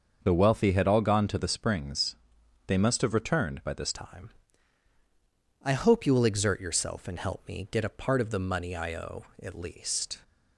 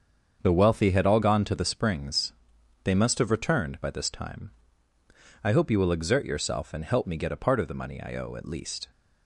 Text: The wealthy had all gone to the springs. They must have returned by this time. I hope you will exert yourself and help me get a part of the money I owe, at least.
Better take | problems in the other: second | starts louder than the rest; until 1.2 s; 6.5 dB; also in the second // changes voice at "time"; from 3.9 s on; 6.2 s long

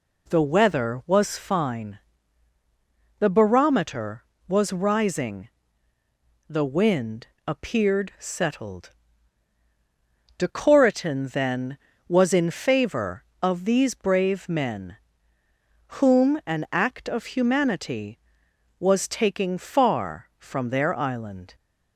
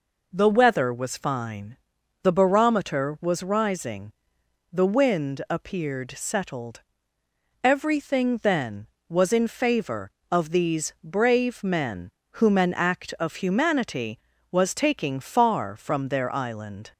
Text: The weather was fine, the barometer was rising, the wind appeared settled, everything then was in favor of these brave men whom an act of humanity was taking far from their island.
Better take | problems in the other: second | pauses between "wind" and "appeared"; slight; at 7.2 s; 0.20 s long // says "decoratin" for "everything"; at 10.3 s // pauses between "men" and "whom"; at 14.9 s; 1.0 s long; slight in the second

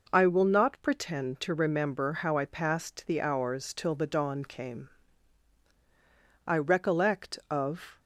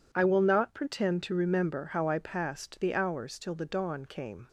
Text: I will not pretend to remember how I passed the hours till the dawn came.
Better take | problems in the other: second | goes on to say "I recollect of"; from 6.4 s on; 1.5 s long

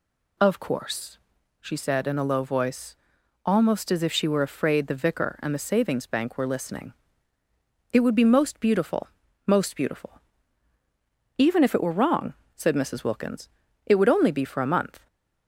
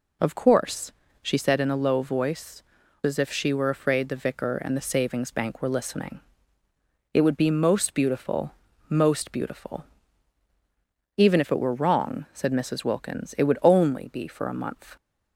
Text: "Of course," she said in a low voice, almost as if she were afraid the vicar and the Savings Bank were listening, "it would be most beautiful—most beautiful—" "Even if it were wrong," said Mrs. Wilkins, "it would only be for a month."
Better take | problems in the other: first | skips "almost"; at 2.8 s

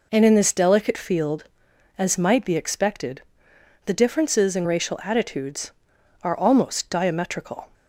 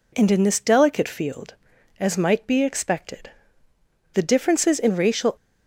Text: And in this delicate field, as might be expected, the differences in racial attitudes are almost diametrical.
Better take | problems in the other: first | stops before "attitudes are almost diametrical"; at 5.3 s

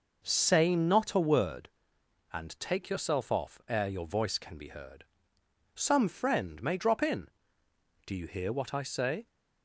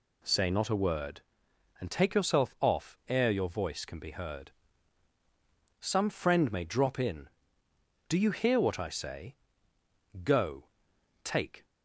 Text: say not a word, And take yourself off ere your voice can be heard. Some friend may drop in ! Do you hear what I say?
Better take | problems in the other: first | goes on to say "Go take"; from 10.2 s on; 1.4 s long

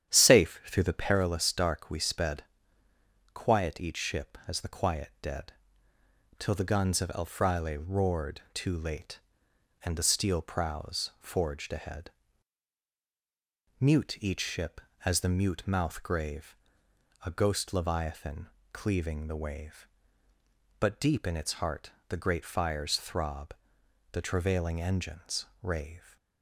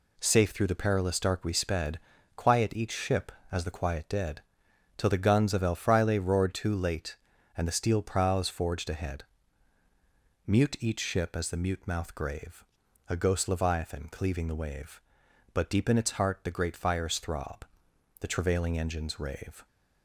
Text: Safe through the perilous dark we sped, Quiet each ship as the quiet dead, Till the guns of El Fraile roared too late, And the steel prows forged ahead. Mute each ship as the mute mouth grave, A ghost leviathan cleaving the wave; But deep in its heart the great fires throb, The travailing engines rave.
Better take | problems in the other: second | starts louder than the rest; strong; until 1.1 s; 9.5 dB // pauses between "leviathan" and "cleaving"; slight; at 18.4 s; 0.24 s long // pauses between "heart" and "the"; slight; at 21.8 s; 0.20 s long // pauses between "engines" and "rave"; slight; at 25.4 s; 0.16 s long

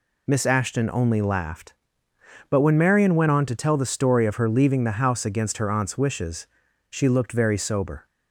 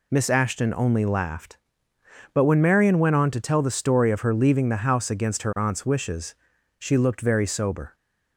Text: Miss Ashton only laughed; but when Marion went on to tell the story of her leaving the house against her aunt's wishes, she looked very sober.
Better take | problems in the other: neither | none

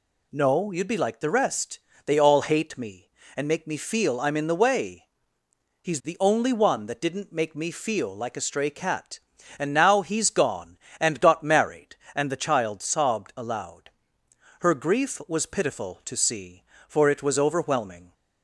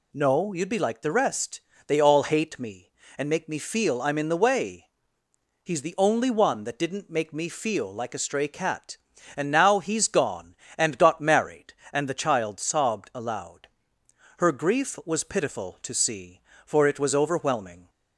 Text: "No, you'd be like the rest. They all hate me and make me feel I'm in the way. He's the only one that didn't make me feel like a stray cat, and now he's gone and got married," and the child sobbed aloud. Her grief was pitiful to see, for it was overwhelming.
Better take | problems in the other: neither | none

